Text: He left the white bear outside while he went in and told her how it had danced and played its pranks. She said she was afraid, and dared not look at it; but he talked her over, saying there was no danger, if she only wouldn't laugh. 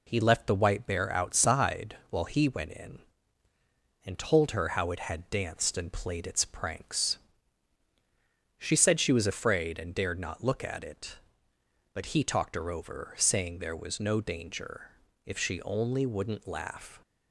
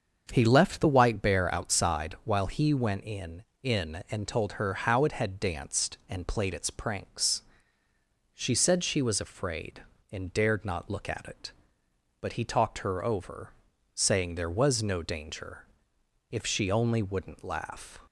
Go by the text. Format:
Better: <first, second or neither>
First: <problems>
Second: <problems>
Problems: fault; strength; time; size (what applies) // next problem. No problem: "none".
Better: first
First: none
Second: starts louder than the rest; until 1.3 s; 7 dB // says "in" twice; at 3.6 s